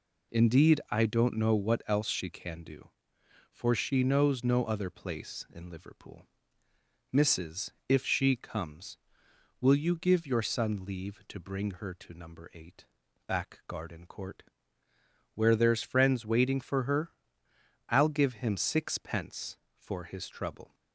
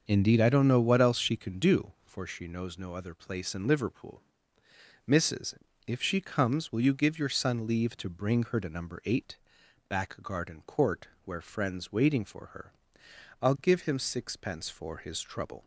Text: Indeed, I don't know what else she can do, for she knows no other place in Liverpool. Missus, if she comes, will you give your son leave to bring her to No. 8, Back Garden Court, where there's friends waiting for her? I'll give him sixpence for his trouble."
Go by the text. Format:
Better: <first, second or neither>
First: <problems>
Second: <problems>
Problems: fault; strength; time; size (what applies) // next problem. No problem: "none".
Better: first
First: none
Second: starts louder than the rest; until 1.0 s; 6.5 dB // skips "there's"; at 11.4 s